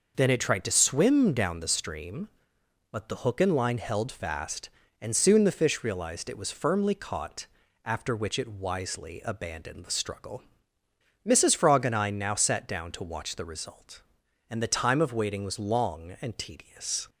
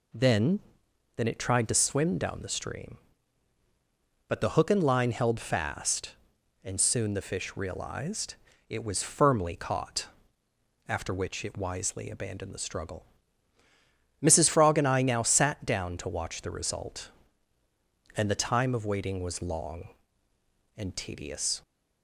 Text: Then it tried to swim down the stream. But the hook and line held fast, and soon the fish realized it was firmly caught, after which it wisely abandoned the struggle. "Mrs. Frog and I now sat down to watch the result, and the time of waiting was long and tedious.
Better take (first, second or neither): first